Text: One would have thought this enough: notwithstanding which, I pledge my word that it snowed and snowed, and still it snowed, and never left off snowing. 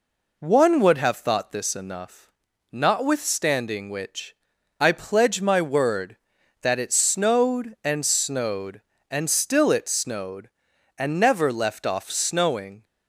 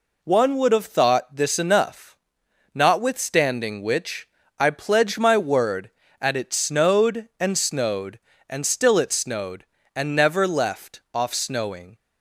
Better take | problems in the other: first | says "at" for "that"; at 6.1 s

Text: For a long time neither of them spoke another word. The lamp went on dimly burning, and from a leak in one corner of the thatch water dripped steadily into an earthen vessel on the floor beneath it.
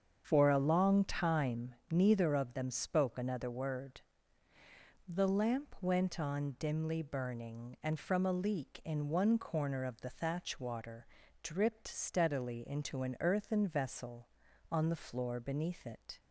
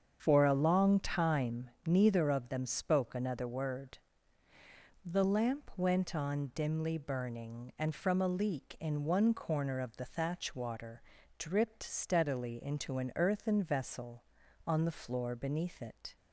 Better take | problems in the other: neither | starts louder than the rest; strong; the same in both // pauses between "time" and "neither"; slight; the same in both // pauses between "water" and "dripped"; slight; the same in both

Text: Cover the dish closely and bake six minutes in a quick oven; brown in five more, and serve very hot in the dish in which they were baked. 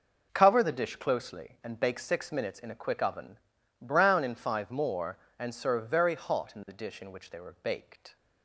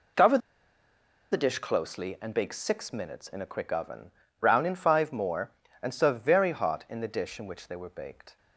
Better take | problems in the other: first | pauses between "Cover" and "the"; noticeable; at 0.3 s; 0.94 s long

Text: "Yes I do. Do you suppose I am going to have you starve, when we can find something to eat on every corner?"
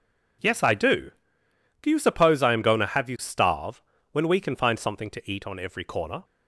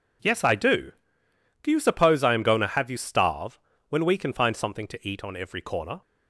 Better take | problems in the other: neither | none

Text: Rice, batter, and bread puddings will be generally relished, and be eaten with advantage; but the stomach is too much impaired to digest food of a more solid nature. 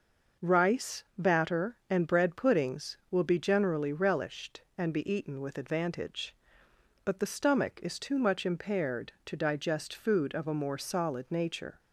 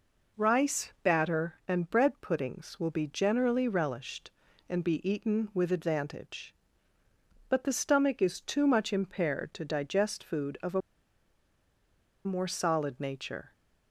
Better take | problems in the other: first | pauses between "a" and "more"; strong; at 10.8 s; 1.4 s long

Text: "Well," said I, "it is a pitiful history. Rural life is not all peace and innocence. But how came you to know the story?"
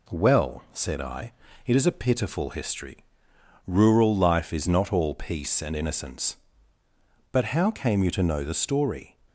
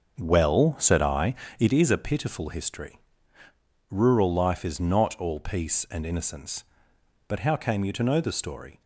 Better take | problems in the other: first | starts louder than the rest; until 1.8 s; 6.5 dB

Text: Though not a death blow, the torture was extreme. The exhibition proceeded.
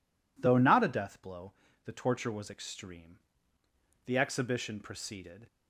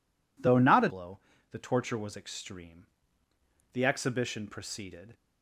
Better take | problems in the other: first | skips "death"; at 0.8 s

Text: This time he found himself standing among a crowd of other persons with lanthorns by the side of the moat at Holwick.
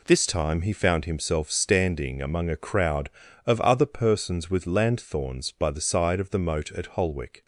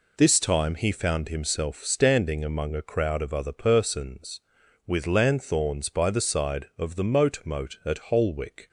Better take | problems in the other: first | says "moat" twice; at 7.4 s

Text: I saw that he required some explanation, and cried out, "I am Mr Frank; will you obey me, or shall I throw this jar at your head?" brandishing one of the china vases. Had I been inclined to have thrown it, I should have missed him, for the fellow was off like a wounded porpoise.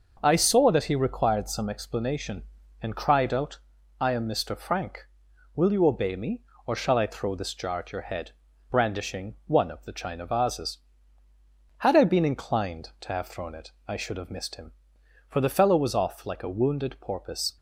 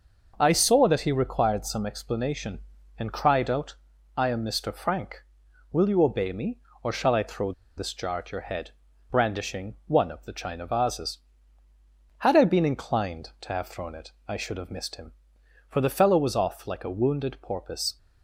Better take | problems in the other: first | pauses between "throw" and "this"; slight; at 7.5 s; 0.24 s long

